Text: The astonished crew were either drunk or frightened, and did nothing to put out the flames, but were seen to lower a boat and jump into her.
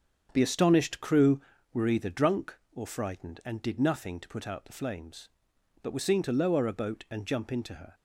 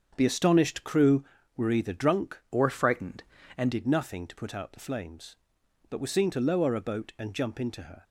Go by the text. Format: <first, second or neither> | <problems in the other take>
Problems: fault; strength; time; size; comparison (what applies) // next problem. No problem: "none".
first | starts louder than the rest; strong; until 1.1 s; 7.5 dB; also in the first // changes voice from "or" to "and"; from 2.5 to 3.7 s; 1.2 s long